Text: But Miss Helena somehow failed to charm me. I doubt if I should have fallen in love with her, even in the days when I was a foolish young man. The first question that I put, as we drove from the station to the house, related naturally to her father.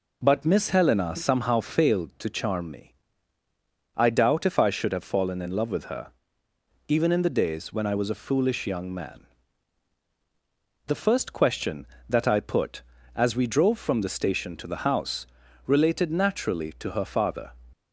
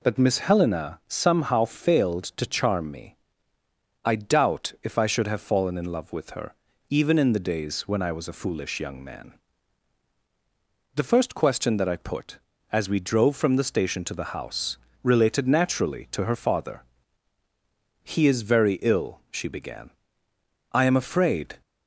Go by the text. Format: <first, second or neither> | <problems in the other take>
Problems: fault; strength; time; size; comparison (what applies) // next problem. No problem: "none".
first | goes on to say "He is very ill she began I am afraid"; strong; from 18.0 s on; 3.5 s long